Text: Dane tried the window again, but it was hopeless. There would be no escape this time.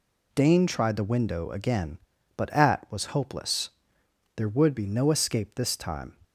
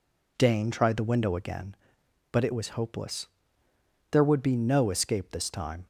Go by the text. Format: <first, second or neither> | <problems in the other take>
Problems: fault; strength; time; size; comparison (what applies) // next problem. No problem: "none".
second | says "at" for "it"; at 2.5 s